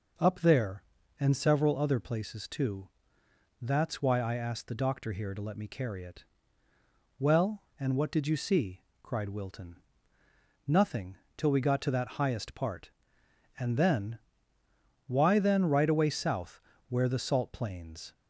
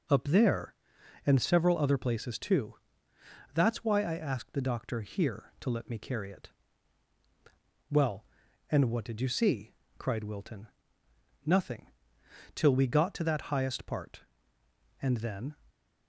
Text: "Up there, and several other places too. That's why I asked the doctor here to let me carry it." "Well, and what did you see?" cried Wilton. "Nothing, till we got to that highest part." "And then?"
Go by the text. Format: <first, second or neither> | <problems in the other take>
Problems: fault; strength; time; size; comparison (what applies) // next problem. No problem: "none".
second | goes on to say "Why then right away south where the salt plains"; strong; from 15.0 s on; 3.0 s long